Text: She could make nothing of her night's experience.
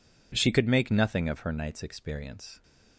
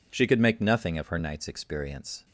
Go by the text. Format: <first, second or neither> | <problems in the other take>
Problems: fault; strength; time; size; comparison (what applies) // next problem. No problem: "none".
neither | none